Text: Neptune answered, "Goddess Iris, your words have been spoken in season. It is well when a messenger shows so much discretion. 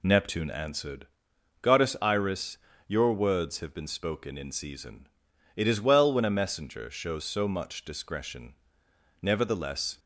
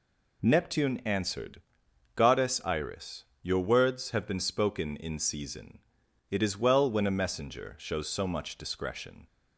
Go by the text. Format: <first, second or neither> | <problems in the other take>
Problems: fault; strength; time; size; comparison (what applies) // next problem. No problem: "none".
second | goes on to say "Nevertheless"; noticeable; from 9.2 s on; 0.78 s long